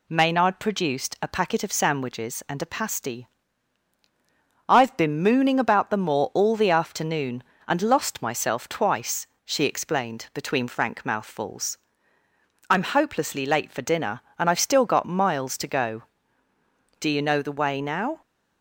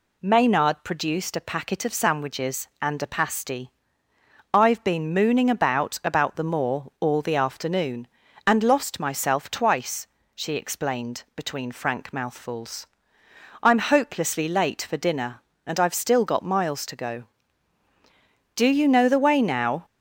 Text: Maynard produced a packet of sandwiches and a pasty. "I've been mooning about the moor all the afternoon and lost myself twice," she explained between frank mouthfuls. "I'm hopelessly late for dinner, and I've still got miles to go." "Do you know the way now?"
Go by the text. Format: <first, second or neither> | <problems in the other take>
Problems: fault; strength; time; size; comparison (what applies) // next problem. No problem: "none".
first | says "about" twice; at 6.0 s